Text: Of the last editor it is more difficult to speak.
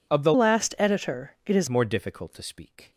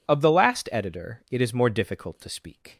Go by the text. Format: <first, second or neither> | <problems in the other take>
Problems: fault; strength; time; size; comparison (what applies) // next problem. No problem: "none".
second | changes voice from "last" to "is"; from 0.3 to 1.6 s; 1.3 s long